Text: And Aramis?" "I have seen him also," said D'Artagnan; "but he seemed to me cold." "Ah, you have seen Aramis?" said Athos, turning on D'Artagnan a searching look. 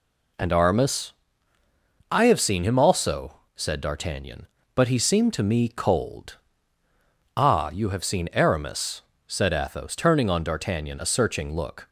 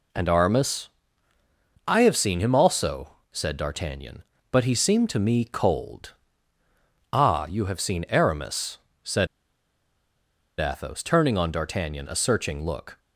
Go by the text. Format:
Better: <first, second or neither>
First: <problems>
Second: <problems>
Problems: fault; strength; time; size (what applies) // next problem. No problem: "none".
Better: first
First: none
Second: pauses between "said" and "Athos"; strong; at 9.2 s; 1.3 s long